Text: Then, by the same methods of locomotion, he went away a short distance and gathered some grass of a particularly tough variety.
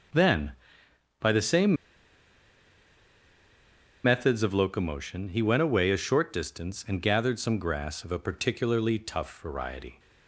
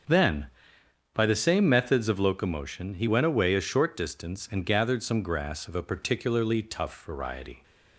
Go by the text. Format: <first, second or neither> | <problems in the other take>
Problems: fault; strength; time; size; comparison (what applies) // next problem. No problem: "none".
second | starts louder than the rest; until 4.1 s; 6.5 dB; also in the second // pauses between "same" and "methods"; strong; at 1.7 s; 2.2 s long